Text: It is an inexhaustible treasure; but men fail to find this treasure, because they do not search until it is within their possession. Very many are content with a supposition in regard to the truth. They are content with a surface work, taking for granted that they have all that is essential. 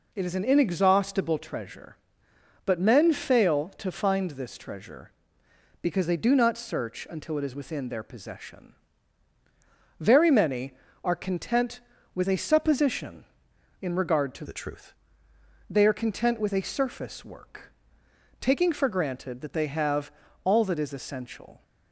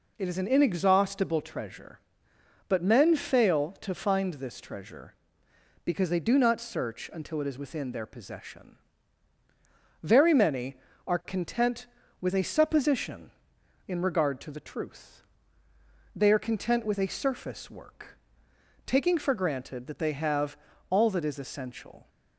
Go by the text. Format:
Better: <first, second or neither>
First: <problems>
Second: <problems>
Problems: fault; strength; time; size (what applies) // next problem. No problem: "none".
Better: second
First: changes voice from "the" to "truth"; from 14.4 to 14.9 s; 0.5 s long // pauses between "have" and "all"; slight; at 20.1 s; 0.34 s long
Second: pauses between "have" and "all"; slight; at 20.5 s; 0.34 s long